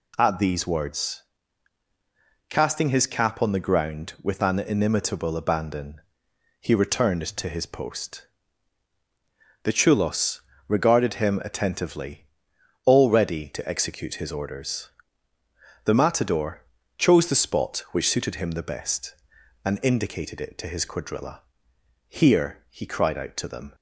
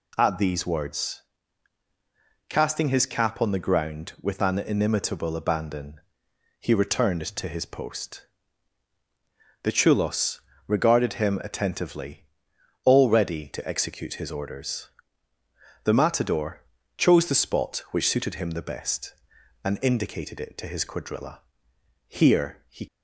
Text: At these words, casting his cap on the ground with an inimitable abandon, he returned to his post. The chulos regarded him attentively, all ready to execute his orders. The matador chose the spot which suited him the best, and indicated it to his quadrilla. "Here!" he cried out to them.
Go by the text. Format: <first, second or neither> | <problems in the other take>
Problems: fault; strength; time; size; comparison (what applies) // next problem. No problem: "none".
first | pauses between "chulos" and "regarded"; slight; at 10.3 s; 0.30 s long; slight in the first // pauses between "matador" and "chose"; slight; at 16.6 s; 0.34 s long; slight in the first // stops before "cried out to them"; at 22.8 s